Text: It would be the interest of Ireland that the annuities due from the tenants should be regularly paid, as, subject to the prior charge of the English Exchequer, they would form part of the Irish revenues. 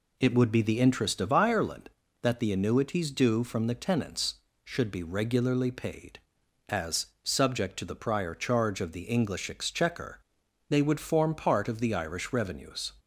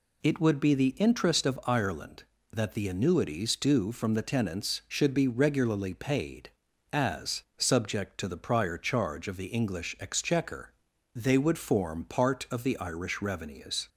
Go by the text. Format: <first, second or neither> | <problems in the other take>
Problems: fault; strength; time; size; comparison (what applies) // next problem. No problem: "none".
neither | none